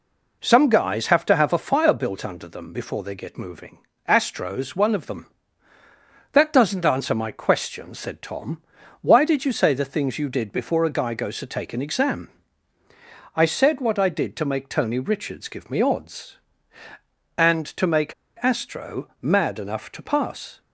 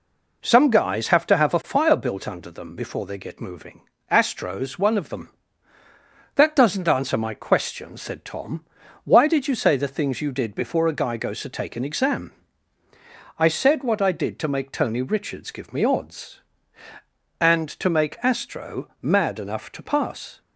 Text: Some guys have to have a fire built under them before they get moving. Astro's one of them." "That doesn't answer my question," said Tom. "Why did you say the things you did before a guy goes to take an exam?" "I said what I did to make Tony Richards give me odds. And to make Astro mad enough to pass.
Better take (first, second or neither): second